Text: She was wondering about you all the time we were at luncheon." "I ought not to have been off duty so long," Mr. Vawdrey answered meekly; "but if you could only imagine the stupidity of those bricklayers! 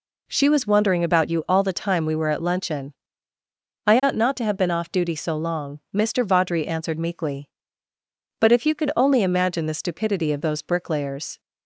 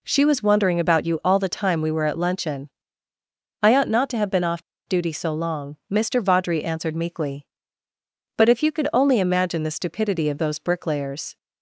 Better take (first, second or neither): first